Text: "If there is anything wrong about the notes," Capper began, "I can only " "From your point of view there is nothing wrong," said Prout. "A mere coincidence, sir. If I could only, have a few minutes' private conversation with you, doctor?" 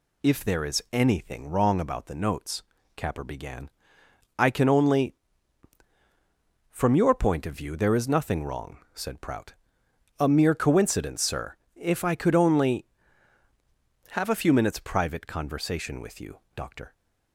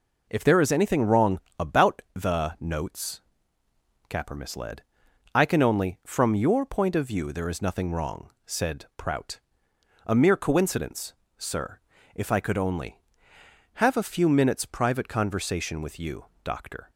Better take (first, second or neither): first